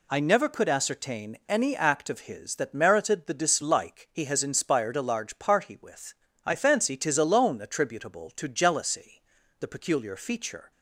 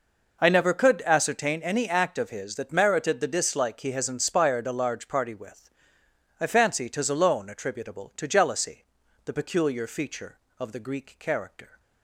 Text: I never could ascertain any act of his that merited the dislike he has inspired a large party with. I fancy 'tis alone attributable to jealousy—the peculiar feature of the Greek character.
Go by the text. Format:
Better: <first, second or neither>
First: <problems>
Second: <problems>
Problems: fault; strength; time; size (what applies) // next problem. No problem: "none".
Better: second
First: stops before "of the Greek character"; at 10.7 s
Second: none